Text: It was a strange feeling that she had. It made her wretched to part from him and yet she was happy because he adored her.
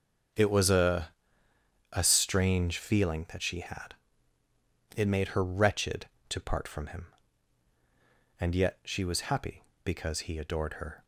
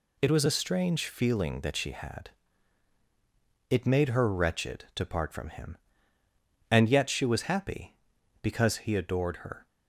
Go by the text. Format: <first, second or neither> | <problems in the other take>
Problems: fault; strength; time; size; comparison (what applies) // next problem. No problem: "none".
second | starts louder than the rest; strong; until 2.2 s; 7 dB // says "a" twice; at 1.9 s